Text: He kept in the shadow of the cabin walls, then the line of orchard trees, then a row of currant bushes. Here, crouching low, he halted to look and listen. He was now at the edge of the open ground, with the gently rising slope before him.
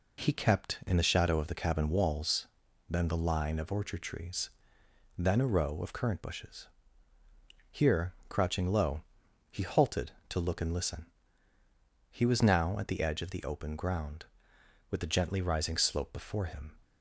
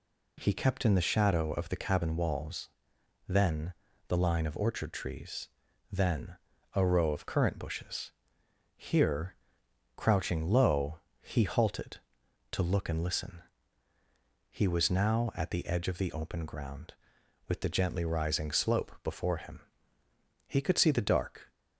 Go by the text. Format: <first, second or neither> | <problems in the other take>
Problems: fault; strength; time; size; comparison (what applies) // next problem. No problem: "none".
first | pauses between "then" and "the"; slight; at 3.7 s; 0.34 s long // pauses between "then" and "a"; at 6.3 s; 0.40 s long // goes on to say "He could see the dark"; noticeable; from 20.4 s on; 1.0 s long